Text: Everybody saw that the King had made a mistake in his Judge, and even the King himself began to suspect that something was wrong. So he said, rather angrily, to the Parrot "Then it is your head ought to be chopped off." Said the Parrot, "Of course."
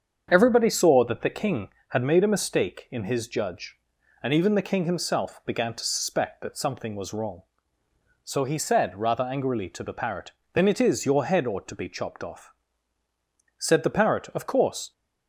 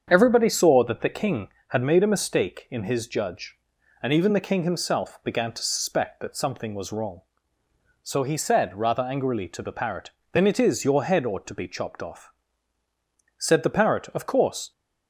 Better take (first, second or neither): neither